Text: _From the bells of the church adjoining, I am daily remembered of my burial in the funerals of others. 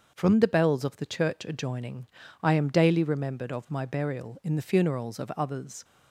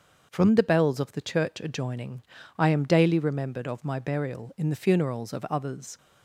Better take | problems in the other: neither | starts louder than the rest; the same in both

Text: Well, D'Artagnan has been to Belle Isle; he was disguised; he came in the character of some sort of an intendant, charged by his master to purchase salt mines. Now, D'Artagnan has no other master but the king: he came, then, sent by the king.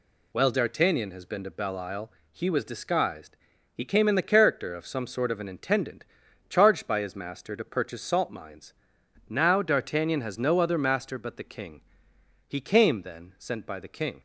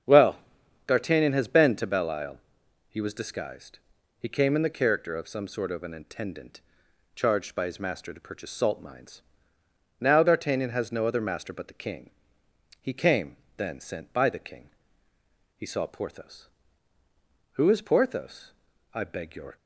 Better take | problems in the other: first | starts louder than the rest; strong; until 1.5 s; 7 dB // goes on to say "He saw Porthos Who is Porthos I beg your"; strong; from 15.5 s on; 4.0 s long

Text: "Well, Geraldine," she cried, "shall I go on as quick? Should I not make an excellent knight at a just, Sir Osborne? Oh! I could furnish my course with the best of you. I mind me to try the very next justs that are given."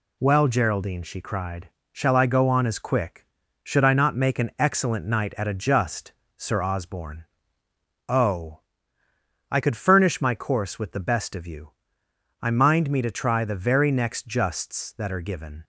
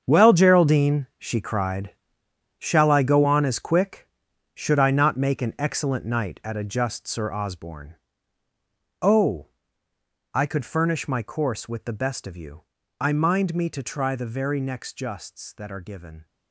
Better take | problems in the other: first | gets quieter; strong; throughout; 12.5 dB

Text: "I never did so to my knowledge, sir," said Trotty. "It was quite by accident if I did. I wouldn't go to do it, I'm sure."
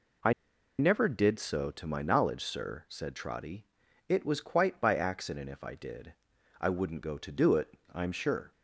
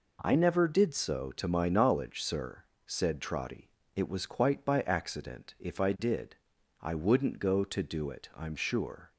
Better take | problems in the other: second | pauses between "I" and "never"; noticeable; at 0.3 s; 0.46 s long

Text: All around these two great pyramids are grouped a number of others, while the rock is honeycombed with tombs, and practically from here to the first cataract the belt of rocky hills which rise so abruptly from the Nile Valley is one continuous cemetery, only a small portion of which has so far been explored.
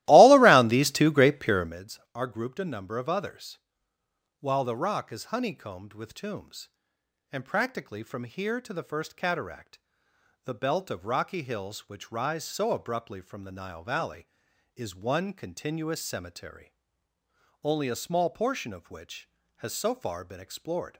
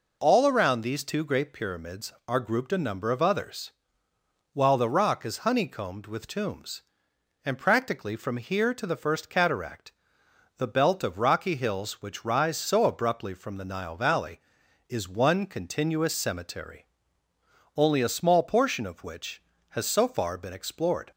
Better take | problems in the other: second | starts louder than the rest; strong; until 1.8 s; 16.5 dB // pauses between "cataract" and "the"; noticeable; at 9.7 s; 0.66 s long; noticeable in the second

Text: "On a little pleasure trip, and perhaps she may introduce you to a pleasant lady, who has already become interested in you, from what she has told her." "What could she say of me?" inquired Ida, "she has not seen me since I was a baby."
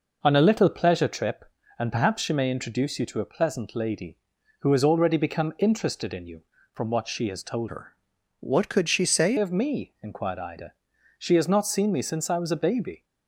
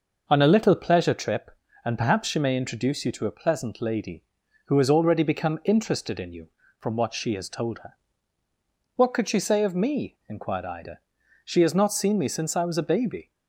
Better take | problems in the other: second | changes voice from "her" to "say"; from 7.6 to 9.3 s; 1.7 s long

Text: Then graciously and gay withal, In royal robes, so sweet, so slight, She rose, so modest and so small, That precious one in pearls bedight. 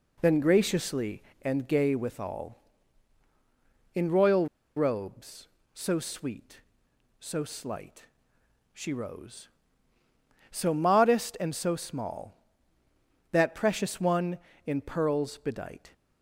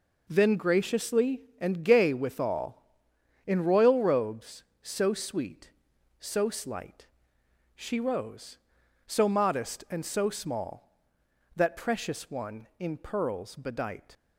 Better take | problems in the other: second | pauses between "royal" and "robes"; slight; at 4.4 s; 0.29 s long

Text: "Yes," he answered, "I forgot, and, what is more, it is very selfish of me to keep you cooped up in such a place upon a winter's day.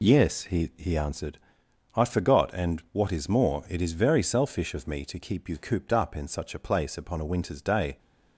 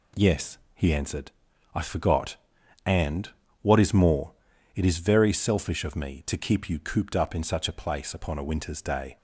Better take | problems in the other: second | says "he" twice; at 0.7 s

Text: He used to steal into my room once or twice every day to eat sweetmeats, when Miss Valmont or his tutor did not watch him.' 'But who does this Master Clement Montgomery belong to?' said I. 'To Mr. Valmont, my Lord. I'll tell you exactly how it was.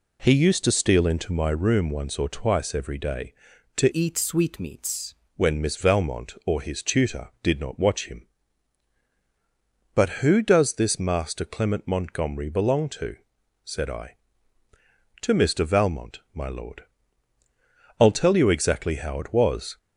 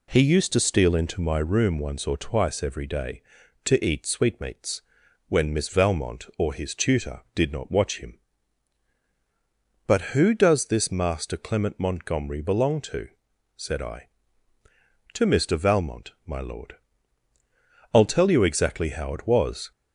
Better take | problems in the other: second | changes voice from "eat" to "sweetmeats"; from 3.9 to 5.1 s; 1.2 s long

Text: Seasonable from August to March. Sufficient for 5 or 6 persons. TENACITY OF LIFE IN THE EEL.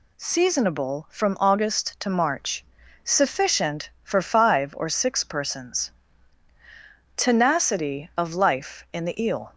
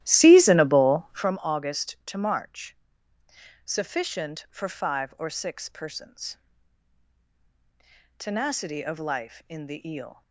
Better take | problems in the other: first | starts louder than the rest; strong; until 1.3 s; 13.5 dB

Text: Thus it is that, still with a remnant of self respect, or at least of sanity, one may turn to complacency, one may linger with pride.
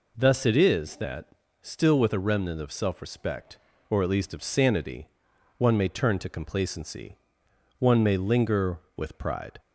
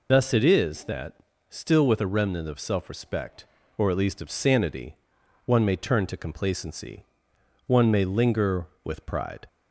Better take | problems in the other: first | loses the start of "Thus"; at 0.0 s; 70 ms

